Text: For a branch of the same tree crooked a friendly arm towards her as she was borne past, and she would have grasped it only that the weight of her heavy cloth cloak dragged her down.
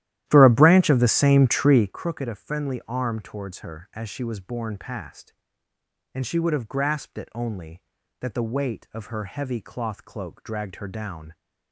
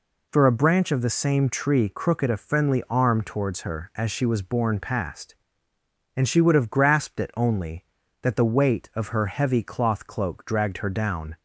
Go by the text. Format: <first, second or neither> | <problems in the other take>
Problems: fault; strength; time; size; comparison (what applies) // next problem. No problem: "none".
second | starts louder than the rest; strong; until 2.0 s; 13 dB